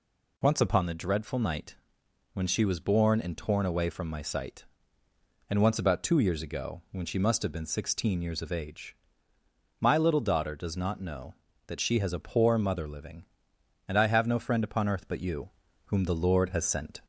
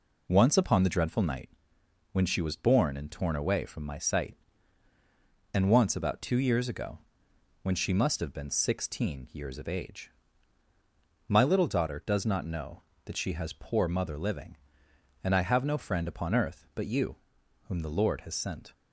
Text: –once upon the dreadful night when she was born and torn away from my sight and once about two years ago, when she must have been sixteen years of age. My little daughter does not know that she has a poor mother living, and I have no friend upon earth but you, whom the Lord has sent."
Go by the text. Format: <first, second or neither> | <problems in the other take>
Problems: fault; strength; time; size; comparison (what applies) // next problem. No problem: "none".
first | pauses between "night" and "when"; noticeable; at 1.4 s; 0.64 s long; noticeable in the first // skips "a"; at 13.5 s